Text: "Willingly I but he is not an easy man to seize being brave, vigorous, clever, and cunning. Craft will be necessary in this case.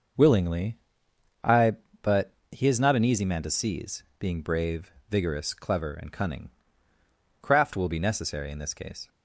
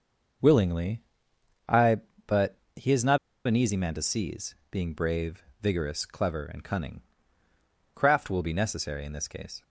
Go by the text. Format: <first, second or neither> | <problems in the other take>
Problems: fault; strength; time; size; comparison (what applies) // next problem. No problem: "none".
first | starts louder than the rest; noticeable; until 2.3 s; 6 dB; also in the first // pauses between "Willingly" and "I"; noticeable; at 1.0 s; 0.66 s long; noticeable in the first // pauses between "but" and "he"; slight; at 2.5 s; 0.18 s long; slight in the first // pauses between "not" and "an"; slight; at 3.1 s; 0.30 s long // pauses between "seize" and "being"; slight; at 4.5 s; 0.16 s long; slight in the first